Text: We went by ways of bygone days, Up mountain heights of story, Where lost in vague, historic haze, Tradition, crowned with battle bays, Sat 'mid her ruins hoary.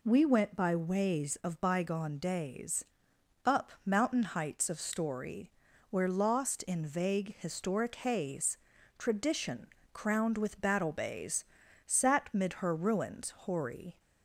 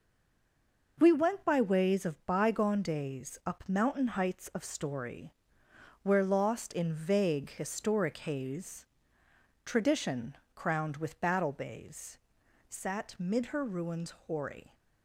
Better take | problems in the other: first | stays silent before the first word; slight; until 0.9 s; 0.9 s long // pauses between "ruins" and "hoary"; slight; at 14.1 s; 0.16 s long

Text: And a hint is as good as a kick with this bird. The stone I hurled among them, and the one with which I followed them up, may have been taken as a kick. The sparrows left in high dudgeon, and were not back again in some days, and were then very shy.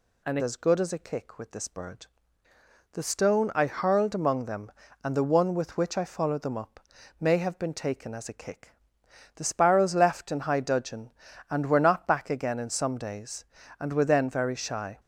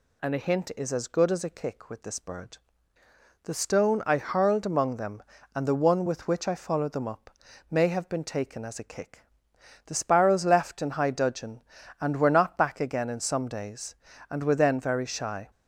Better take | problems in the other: second | skips "a hint is"; at 0.3 s

